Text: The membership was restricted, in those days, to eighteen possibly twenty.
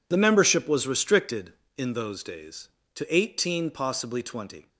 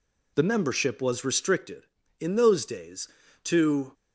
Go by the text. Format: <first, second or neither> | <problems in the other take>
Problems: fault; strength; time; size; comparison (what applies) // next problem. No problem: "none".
first | stops before "eighteen possibly twenty"; at 3.9 s